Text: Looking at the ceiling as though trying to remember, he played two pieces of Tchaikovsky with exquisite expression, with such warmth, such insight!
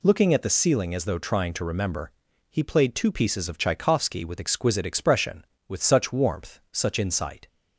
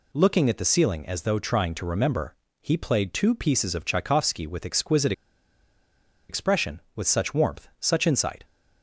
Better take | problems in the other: first | pauses between "exquisite" and "expression"; at 5.1 s; 1.1 s long

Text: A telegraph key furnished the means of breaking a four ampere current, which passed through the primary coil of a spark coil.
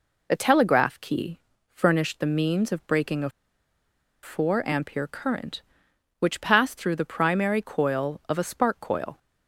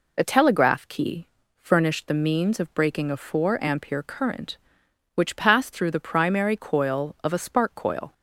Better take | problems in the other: second | pauses between "key" and "furnished"; slight; at 1.3 s; 0.32 s long; slight in the second // pauses between "a" and "four"; noticeable; at 3.3 s; 0.92 s long

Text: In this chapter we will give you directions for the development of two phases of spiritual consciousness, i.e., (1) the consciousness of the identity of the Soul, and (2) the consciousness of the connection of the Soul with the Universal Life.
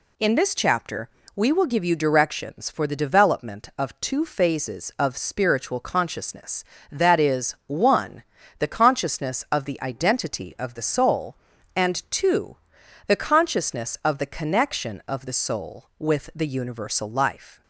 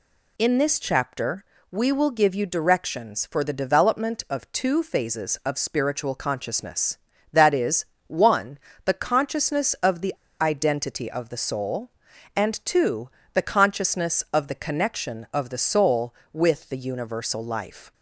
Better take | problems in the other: first | pauses between "chapter" and "we"; slight; at 1.4 s; 0.26 s long; slight in the first // pauses between "the" and "identity"; slight; at 10.1 s; 0.28 s long

